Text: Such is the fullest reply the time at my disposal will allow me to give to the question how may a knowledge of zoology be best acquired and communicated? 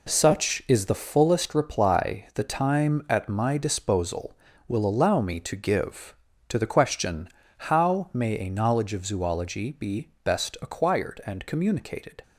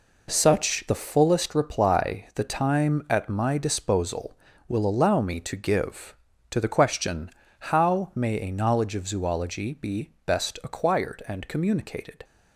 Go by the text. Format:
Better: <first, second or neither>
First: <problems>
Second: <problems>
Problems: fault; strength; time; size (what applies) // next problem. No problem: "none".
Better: first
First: pauses between "question" and "how"; slight; at 7.2 s; 0.30 s long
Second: skips "is"; at 0.8 s // pauses between "question" and "how"; slight; at 7.2 s; 0.30 s long